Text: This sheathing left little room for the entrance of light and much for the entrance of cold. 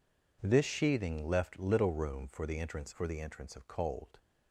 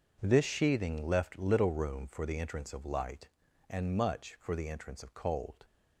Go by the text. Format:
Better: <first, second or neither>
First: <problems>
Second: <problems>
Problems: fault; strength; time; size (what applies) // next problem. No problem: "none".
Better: second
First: skips "of light and much"; at 2.9 s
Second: none